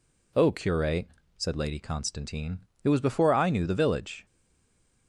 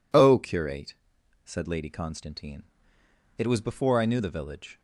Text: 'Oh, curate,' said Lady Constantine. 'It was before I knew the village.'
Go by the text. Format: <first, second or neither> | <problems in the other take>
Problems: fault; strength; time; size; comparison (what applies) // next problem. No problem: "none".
second | stays silent after the last word; slight; from 4.2 s on; 0.8 s long